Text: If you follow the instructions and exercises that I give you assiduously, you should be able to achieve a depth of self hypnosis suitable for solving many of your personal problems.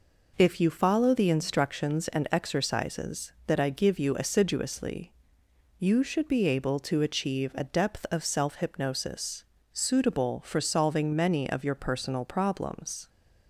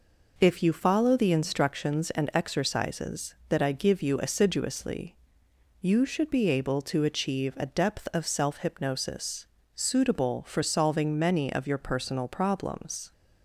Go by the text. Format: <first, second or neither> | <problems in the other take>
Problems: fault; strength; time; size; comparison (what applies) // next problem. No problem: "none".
neither | pauses between "hypnosis" and "suitable"; slight; the same in both